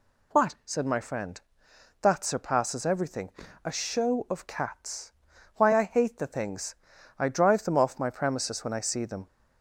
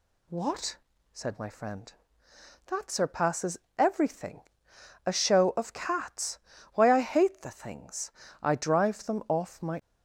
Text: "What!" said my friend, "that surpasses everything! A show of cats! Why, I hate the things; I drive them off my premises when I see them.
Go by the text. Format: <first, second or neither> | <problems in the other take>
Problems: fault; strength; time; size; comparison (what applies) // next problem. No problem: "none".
first | pauses between "surpasses" and "everything"; slight; at 3.5 s; 0.18 s long // stops before "premises when I see them"; at 9.7 s